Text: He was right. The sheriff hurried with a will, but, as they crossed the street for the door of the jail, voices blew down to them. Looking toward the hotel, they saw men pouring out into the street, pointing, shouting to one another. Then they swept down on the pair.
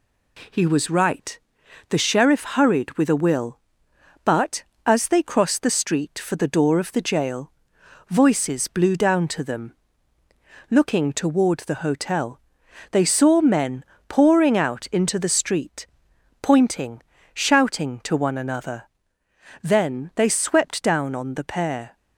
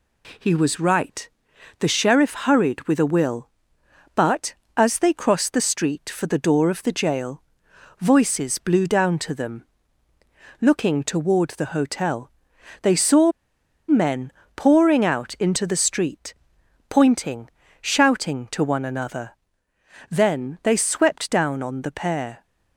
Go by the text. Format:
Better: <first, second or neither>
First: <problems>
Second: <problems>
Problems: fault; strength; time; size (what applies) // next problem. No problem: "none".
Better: first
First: pauses between "men" and "pouring"; slight; at 13.8 s; 0.22 s long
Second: pauses between "saw" and "men"; noticeable; at 13.3 s; 0.57 s long // pauses between "men" and "pouring"; slight; at 14.3 s; 0.22 s long